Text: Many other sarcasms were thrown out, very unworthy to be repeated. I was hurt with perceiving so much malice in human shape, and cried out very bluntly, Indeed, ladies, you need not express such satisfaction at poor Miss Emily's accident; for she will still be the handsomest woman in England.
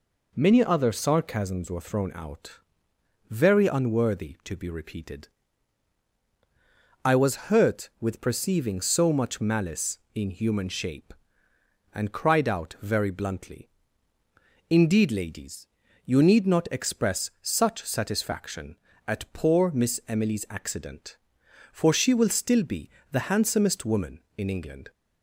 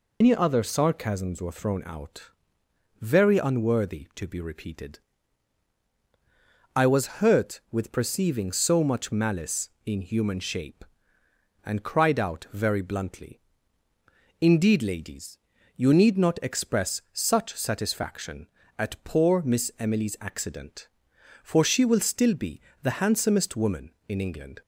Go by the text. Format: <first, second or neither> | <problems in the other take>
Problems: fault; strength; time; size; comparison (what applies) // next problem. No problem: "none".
first | loses the start of "Many"; at 0.2 s; 145 ms // pauses between "be" and "the"; slight; at 22.5 s; 0.22 s long; slight in the first